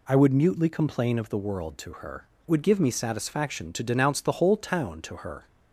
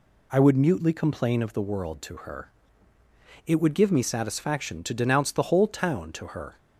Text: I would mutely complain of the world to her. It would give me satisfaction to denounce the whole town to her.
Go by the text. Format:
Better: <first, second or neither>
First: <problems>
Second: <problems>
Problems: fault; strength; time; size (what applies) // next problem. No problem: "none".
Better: second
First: skips "It"; at 2.3 s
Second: none